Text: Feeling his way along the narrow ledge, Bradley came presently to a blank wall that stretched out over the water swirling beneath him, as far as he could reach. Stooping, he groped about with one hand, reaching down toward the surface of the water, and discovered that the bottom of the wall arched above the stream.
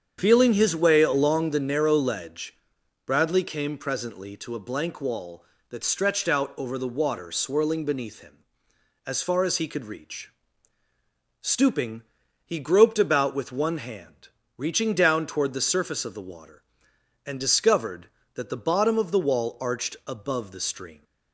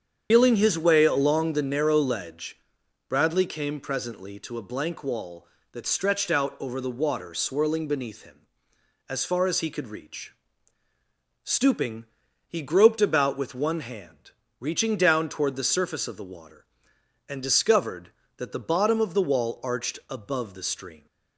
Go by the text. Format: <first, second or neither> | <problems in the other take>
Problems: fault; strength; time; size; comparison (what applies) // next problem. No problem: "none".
first | loses the start of "Feeling"; at 0.3 s; 95 ms // starts louder than the rest; strong; until 1.3 s; 8 dB; strong in the first